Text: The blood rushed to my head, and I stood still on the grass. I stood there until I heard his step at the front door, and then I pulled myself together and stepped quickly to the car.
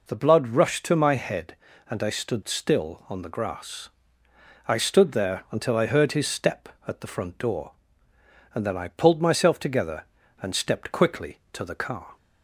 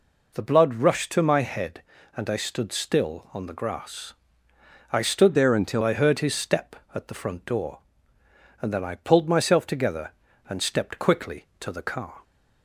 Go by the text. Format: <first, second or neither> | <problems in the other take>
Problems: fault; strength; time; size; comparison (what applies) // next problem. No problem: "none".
first | changes voice from "there" to "until"; from 5.3 to 5.8 s; 0.5 s long